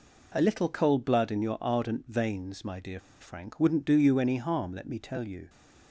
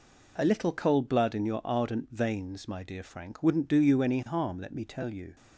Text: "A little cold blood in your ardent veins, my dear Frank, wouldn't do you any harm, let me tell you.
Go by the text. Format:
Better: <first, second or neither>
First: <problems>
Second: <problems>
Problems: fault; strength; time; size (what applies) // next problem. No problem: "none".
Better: second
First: pauses between "dear" and "Frank"; slight; at 2.9 s; 0.21 s long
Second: none